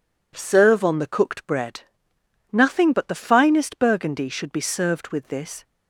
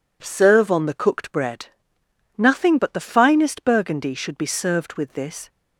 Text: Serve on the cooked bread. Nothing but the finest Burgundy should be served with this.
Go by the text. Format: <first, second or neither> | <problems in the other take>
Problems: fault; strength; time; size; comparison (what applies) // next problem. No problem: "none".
neither | none